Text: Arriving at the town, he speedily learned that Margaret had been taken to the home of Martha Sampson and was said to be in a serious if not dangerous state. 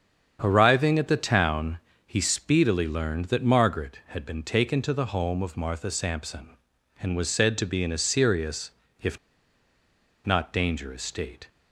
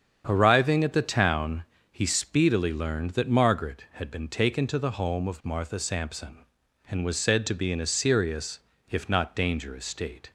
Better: second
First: starts louder than the rest; strong; until 1.4 s; 7.5 dB // pauses between "serious" and "if"; slight; at 8.7 s; 0.32 s long // pauses between "if" and "not"; at 9.1 s; 1.0 s long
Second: starts louder than the rest; strong; until 1.2 s; 7.5 dB // pauses between "serious" and "if"; slight; at 8.5 s; 0.32 s long

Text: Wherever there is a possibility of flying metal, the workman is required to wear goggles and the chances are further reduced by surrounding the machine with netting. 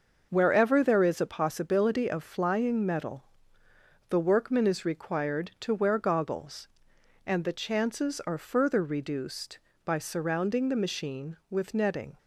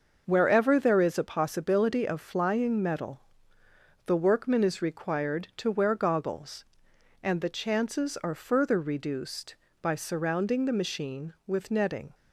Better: neither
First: starts louder than the rest; until 1.3 s; 6 dB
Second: starts louder than the rest; until 1.2 s; 6 dB

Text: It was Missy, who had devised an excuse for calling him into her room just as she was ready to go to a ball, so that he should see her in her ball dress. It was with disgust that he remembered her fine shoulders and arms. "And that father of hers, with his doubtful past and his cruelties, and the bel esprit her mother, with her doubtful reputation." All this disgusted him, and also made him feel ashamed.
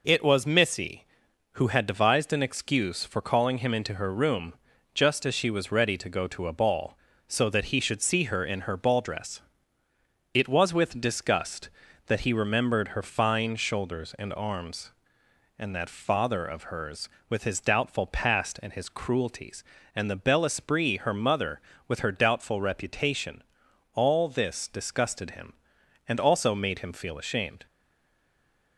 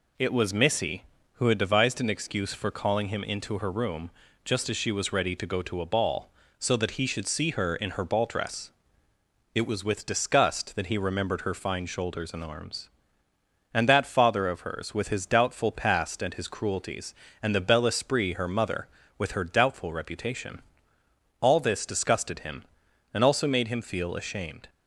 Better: second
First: pauses between "room" and "just"; at 4.5 s; 0.40 s long // stays silent after the last word; from 27.6 s on; 1.1 s long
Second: pauses between "room" and "just"; slight; at 4.1 s; 0.34 s long

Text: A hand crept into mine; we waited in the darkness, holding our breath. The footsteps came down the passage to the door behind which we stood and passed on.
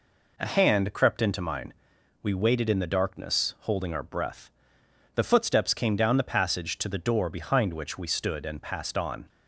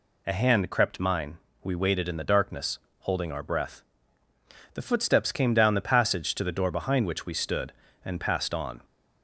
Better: first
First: none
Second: skips "into"; at 0.9 s

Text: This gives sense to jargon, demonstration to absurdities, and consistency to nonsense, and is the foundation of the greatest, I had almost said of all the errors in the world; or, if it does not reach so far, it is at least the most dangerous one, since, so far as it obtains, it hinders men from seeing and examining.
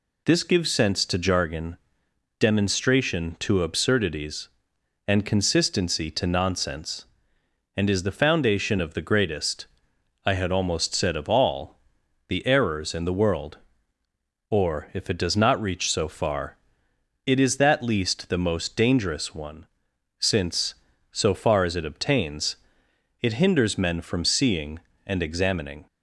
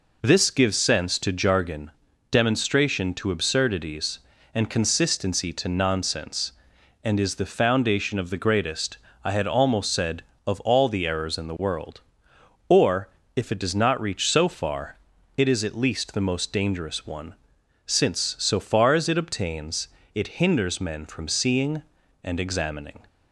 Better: second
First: pauses between "all" and "the"; noticeable; at 11.7 s; 0.48 s long // says "that" for "at"; at 17.5 s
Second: none

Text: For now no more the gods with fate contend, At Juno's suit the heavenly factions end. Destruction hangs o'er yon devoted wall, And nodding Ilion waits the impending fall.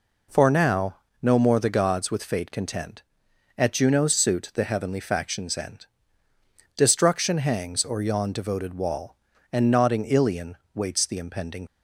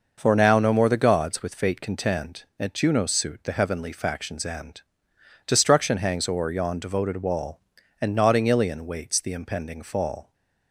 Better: second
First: pauses between "now" and "no"; slight; at 0.9 s; 0.24 s long // pauses between "Ilion" and "waits"; slight; at 10.5 s; 0.18 s long // stops before "fall"; at 11.6 s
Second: none

